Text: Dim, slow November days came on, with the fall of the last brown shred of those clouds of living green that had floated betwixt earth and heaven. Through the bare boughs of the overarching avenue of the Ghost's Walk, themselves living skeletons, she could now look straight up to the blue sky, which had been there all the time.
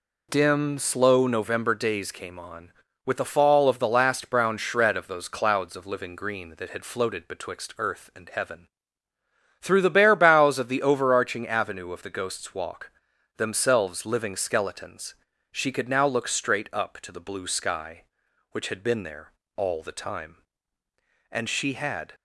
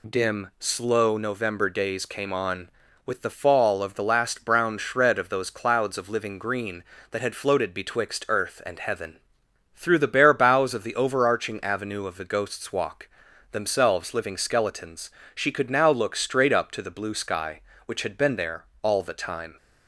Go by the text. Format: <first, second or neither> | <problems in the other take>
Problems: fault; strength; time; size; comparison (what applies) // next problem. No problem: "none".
second | pauses between "there" and "all"; slight; at 19.3 s; 0.24 s long; slight in the second // goes on to say "And she had"; noticeable; from 21.3 s on; 0.82 s long